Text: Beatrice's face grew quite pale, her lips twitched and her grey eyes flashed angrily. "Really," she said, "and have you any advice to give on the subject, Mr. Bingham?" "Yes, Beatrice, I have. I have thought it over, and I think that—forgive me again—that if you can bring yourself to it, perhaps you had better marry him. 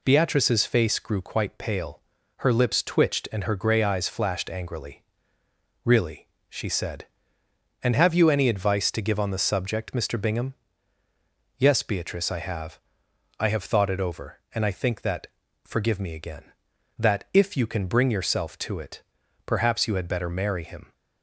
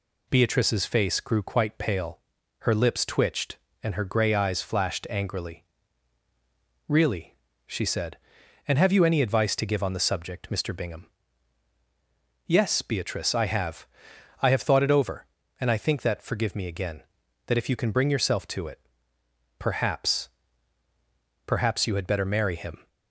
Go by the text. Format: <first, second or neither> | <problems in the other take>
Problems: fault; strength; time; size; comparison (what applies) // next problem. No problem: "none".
first | says "perhaps" twice; at 21.4 s